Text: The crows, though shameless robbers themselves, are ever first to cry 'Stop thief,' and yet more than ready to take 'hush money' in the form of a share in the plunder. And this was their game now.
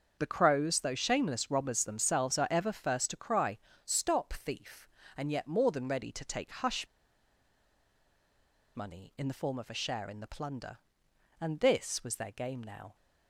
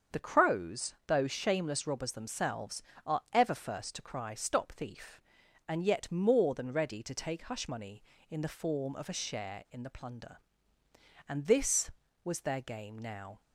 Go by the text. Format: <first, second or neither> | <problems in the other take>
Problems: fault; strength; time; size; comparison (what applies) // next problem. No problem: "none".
second | starts louder than the rest; until 1.2 s; 6.5 dB; also in the second // pauses between "cry" and "Stop"; slight; at 3.5 s; 0.28 s long // pauses between "hush" and "money"; strong; at 6.8 s; 1.8 s long